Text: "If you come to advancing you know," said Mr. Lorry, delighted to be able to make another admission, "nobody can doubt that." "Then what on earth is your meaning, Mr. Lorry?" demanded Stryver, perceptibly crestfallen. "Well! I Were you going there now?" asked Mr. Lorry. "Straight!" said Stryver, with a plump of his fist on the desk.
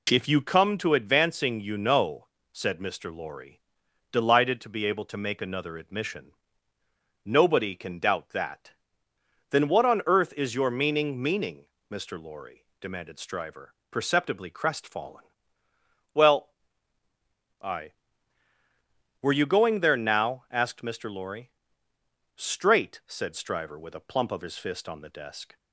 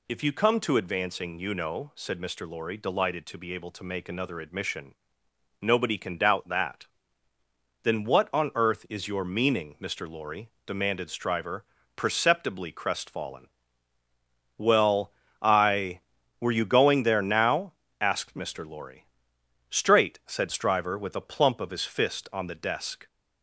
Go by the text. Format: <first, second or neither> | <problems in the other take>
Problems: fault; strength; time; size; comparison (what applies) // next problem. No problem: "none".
second | says "meaning" twice; at 11.2 s